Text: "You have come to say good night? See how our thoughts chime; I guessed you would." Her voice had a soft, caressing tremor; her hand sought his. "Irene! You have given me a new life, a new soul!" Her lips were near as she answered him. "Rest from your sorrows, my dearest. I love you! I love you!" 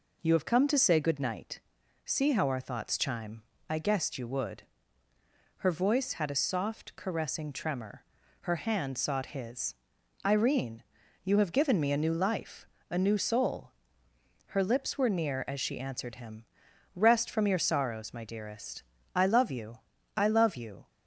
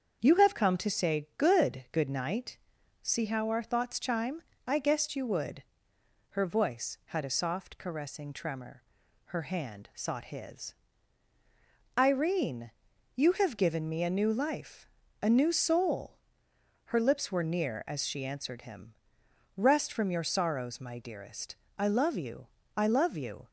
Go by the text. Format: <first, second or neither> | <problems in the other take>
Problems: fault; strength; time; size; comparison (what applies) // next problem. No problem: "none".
first | starts louder than the rest; strong; until 1.2 s; 7.5 dB // says "good" twice; at 1.9 s